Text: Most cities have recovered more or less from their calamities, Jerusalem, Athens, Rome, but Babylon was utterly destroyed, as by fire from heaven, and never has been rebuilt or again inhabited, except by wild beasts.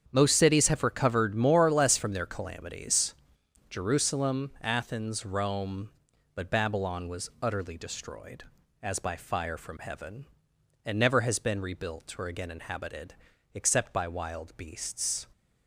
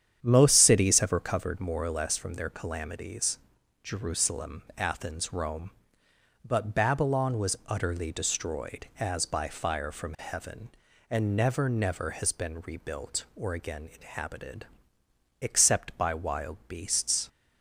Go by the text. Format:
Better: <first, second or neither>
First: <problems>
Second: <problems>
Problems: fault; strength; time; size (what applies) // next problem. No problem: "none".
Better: first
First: starts louder than the rest; strong; until 1.1 s; 8 dB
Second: starts louder than the rest; strong; until 1.2 s; 9 dB // says "never" twice; at 11.6 s